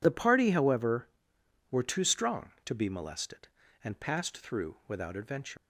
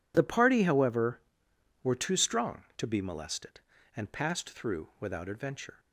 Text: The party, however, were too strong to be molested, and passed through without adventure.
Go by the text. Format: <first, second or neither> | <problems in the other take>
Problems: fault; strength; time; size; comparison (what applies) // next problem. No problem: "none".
second | leaves "adventure" unfinished; at 5.5 s; 100 ms